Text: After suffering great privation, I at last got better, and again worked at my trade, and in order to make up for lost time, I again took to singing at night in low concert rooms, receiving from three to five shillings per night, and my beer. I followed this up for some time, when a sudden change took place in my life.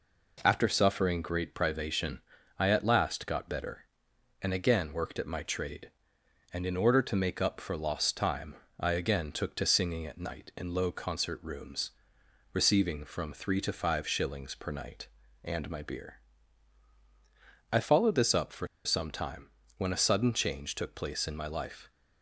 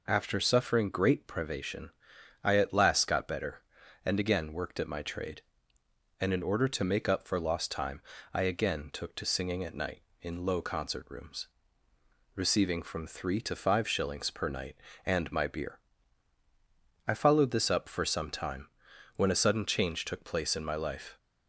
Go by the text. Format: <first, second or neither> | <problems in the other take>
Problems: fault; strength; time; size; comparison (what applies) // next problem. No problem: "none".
second | pauses between "for" and "some"; slight; at 18.6 s; 0.18 s long